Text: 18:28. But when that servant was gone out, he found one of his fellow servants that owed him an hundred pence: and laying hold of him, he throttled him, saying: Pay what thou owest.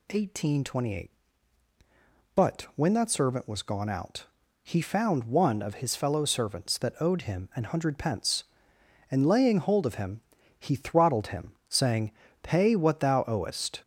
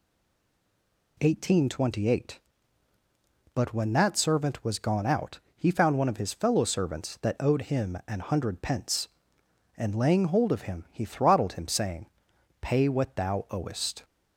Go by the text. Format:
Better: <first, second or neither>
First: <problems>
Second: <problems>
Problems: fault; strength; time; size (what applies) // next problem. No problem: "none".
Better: first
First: none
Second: stays silent before the first word; until 1.1 s; 1.1 s long